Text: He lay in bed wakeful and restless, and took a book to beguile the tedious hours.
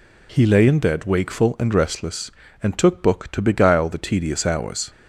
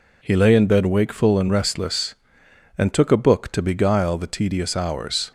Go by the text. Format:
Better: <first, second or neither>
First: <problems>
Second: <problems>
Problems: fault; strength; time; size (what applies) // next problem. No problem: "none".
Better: second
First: skips "a"; at 3.0 s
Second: none